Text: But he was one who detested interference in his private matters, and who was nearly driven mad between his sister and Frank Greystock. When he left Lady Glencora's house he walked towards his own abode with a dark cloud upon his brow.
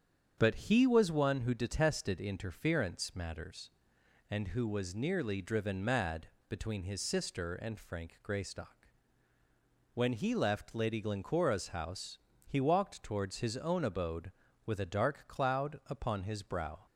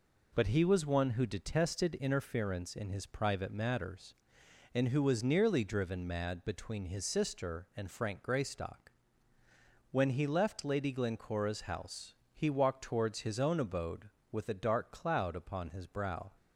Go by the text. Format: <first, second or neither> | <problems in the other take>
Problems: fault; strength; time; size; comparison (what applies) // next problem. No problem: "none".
second | starts louder than the rest; strong; until 1.3 s; 8 dB // skips "in his private"; at 3.1 s // pauses between "mad" and "between"; slight; at 6.2 s; 0.20 s long // pauses between "house" and "he"; slight; at 12.1 s; 0.30 s long; slight in the second